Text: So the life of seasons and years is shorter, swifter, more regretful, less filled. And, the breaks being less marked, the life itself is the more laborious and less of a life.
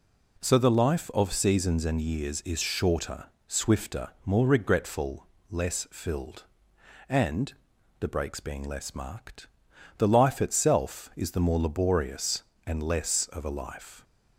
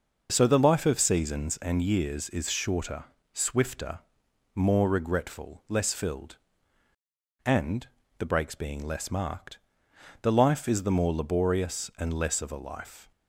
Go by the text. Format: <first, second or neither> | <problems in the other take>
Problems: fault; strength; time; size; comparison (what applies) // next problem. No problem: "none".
first | skips "itself"; at 10.6 s